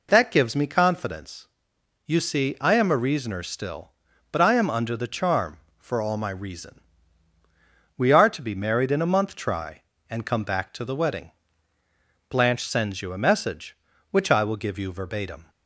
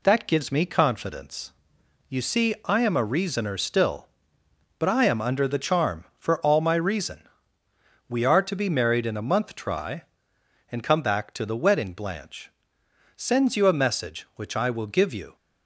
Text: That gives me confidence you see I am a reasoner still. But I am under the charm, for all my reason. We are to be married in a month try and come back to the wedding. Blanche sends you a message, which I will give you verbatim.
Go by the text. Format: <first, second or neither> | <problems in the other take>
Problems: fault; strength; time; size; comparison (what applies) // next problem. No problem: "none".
first | pauses between "confidence" and "you"; noticeable; at 1.5 s; 0.58 s long; noticeable in the first // pauses between "Blanche" and "sends"; noticeable; at 12.5 s; 0.64 s long // stops before "verbatim"; at 15.3 s